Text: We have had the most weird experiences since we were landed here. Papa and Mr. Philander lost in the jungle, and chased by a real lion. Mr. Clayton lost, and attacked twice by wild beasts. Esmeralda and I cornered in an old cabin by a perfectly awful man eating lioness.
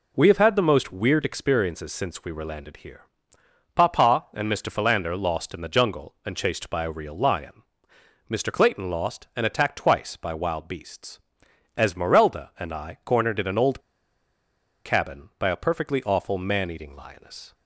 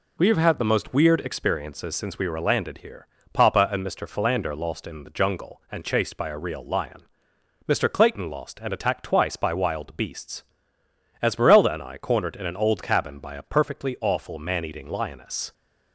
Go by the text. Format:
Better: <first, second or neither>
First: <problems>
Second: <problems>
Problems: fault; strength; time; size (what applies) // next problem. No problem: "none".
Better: second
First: pauses between "old" and "cabin"; at 13.8 s; 1.0 s long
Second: none